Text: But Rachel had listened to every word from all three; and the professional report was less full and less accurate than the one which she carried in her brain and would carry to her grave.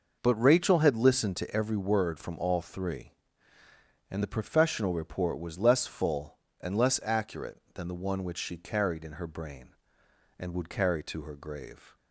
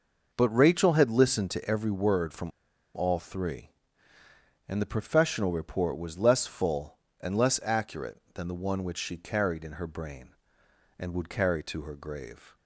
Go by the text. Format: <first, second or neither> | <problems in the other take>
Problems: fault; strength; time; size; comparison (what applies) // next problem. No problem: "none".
first | pauses between "from" and "all"; noticeable; at 2.5 s; 0.47 s long